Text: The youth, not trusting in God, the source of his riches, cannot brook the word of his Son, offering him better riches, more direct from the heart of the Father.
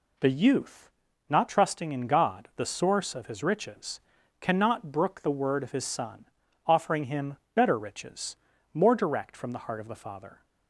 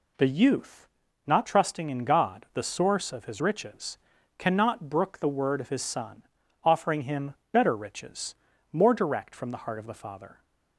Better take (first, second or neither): neither